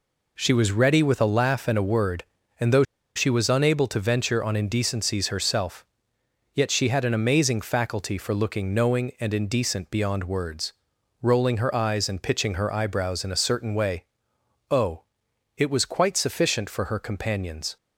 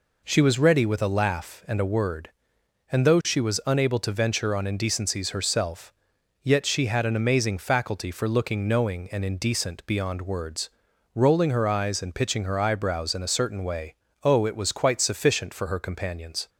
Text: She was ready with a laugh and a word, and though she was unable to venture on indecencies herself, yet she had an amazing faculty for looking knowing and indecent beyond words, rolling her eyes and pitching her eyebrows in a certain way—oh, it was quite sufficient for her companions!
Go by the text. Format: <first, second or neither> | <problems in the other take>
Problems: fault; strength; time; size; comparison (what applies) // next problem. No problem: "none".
second | pauses between "though" and "she"; slight; at 2.8 s; 0.32 s long